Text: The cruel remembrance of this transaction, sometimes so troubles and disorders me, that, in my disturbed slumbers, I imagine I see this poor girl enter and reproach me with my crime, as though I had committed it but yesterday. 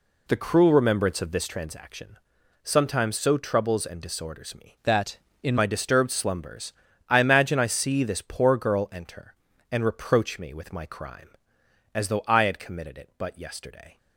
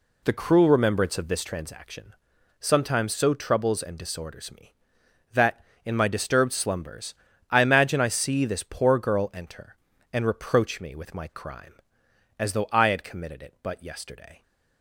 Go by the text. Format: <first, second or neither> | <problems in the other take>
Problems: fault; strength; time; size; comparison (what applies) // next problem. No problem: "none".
second | changes voice from "that" to "in"; from 4.8 to 5.5 s; 0.7 s long